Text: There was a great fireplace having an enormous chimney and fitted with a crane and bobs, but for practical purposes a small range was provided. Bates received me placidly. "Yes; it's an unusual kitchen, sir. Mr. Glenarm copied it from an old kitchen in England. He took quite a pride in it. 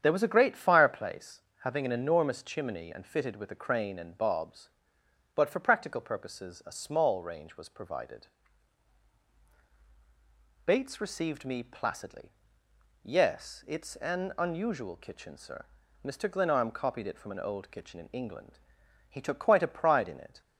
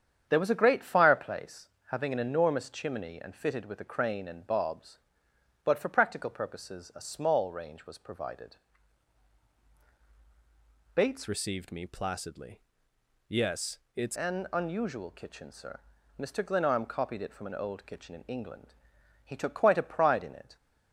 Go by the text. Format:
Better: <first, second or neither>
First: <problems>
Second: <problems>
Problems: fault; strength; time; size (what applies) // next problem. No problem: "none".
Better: first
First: starts louder than the rest; strong; until 1.0 s; 8.5 dB // pauses between "fireplace" and "having"; slight; at 1.4 s; 0.22 s long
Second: starts louder than the rest; strong; until 1.3 s; 8.5 dB // pauses between "fireplace" and "having"; slight; at 1.6 s; 0.22 s long // changes voice from "received" to "it's"; from 11.2 to 14.1 s; 2.9 s long